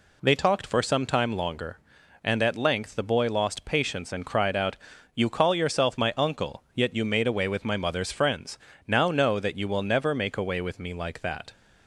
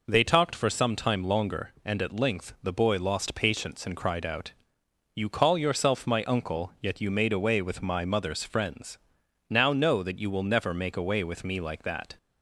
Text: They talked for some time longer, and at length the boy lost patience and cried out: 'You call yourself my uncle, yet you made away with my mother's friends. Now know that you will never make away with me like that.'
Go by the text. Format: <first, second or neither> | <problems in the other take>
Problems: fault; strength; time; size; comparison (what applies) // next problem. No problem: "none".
neither | none